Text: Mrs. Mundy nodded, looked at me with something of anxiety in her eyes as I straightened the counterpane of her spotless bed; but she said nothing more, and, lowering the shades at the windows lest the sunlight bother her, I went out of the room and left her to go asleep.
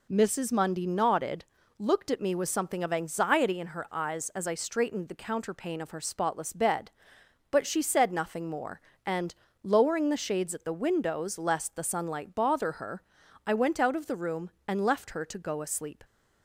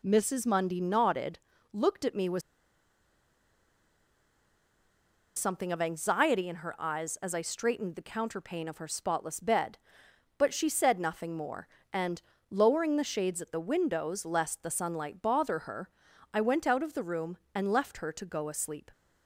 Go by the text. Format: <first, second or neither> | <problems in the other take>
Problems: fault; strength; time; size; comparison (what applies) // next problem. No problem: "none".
first | pauses between "with" and "something"; strong; at 2.4 s; 2.9 s long